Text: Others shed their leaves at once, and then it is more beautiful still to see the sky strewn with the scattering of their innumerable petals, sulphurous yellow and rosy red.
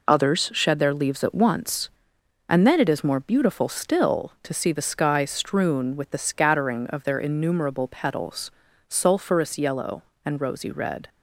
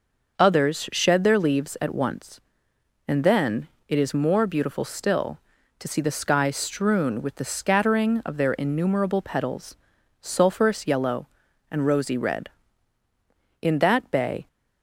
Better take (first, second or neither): first